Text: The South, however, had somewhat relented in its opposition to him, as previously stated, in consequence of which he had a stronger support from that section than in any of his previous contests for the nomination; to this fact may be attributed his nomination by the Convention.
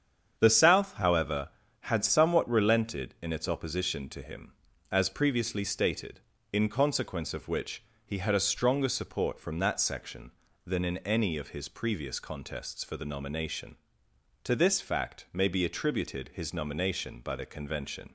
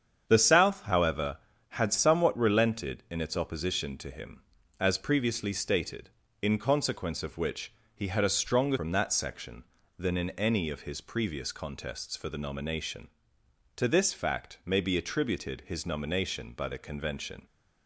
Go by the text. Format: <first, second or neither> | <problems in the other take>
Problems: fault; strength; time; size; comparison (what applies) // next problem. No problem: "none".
first | starts louder than the rest; strong; until 1.2 s; 8 dB; strong in the first // pauses between "which" and "he"; slight; at 7.7 s; 0.22 s long; slight in the first // skips "support"; at 8.7 s